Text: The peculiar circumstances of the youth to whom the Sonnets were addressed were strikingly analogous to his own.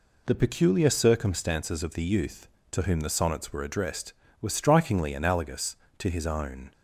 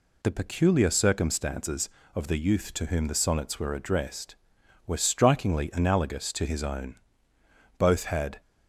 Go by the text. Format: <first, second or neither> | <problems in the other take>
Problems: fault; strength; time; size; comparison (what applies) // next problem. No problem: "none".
first | goes on to say "Both had"; noticeable; from 7.7 s on; 0.62 s long